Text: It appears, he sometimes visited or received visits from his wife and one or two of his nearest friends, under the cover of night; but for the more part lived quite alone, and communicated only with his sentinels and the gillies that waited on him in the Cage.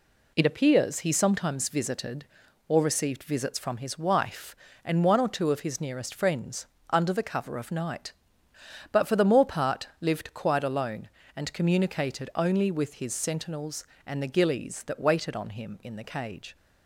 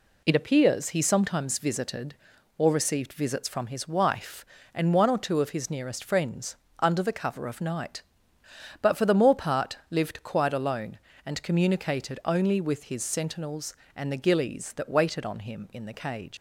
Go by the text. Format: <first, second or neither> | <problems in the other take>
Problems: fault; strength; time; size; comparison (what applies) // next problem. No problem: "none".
first | leaves "Cage" unfinished; at 16.3 s; 80 ms